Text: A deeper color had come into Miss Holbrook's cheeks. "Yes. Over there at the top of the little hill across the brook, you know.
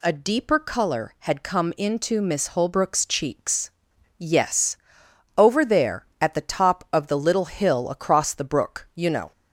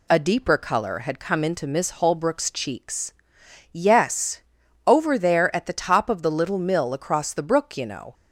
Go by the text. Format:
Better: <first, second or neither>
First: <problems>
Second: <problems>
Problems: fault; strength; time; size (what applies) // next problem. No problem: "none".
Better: first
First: none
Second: says "mill" for "hill"; at 6.5 s